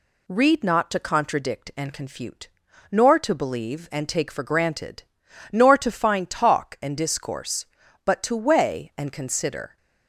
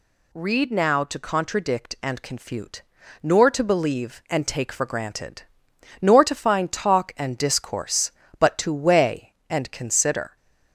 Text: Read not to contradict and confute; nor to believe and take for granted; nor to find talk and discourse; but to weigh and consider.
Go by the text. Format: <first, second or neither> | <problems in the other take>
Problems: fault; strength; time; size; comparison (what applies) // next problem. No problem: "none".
first | says "now" for "not"; at 0.6 s